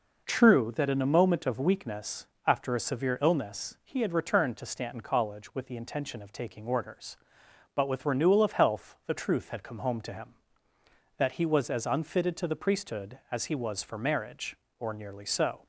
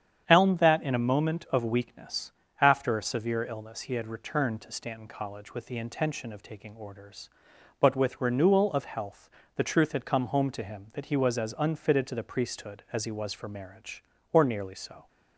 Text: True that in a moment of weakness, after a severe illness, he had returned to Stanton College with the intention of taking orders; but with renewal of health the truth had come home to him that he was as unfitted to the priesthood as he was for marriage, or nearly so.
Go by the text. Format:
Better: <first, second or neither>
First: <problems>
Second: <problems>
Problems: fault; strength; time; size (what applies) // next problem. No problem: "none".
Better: first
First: none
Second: starts louder than the rest; strong; until 1.2 s; 8.5 dB // says "Elm" for "True"; at 0.2 s // pauses between "health" and "the"; slight; at 9.2 s; 0.26 s long